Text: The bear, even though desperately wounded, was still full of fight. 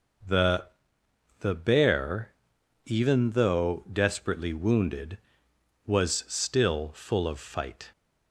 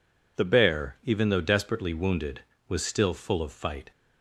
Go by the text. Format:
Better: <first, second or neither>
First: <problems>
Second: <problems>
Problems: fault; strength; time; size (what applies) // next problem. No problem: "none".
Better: second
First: says "The" twice; at 1.3 s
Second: none